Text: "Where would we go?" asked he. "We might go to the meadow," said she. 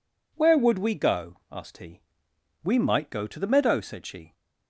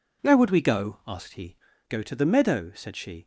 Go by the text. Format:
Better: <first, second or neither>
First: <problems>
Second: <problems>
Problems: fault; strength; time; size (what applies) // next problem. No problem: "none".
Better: first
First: none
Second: skips "We might"; at 1.7 s